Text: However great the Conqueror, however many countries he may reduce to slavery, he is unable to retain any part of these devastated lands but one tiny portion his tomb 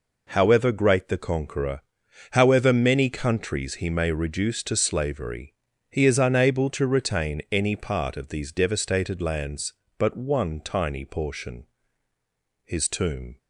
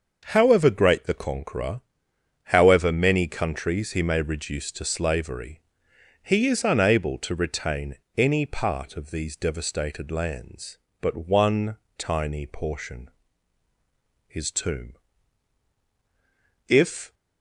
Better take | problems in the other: first | starts louder than the rest; until 1.2 s; 6.5 dB // pauses between "retain" and "any"; slight; at 7.9 s; 0.20 s long // pauses between "one" and "tiny"; slight; at 11.7 s; 0.22 s long // pauses between "portion" and "his"; at 13.0 s; 1.1 s long; also in the first // goes on to say "If"; slight; from 16.6 s on; 0.46 s long

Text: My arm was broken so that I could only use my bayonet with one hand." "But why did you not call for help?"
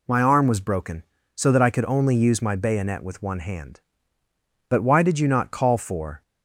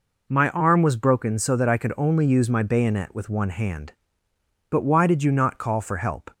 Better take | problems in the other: second | stops before "help"; at 6.2 s

